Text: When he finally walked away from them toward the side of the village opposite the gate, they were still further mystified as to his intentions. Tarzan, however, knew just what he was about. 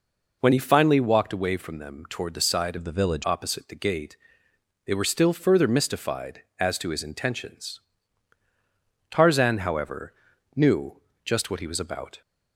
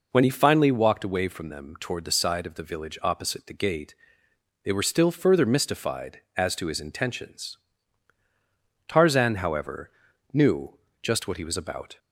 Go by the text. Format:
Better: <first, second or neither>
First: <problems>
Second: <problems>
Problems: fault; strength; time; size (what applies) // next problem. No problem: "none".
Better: second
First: changes voice from "of" to "village"; from 2.7 to 3.2 s; 0.5 s long // pauses between "knew" and "just"; slight; at 10.9 s; 0.26 s long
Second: pauses between "knew" and "just"; slight; at 10.7 s; 0.26 s long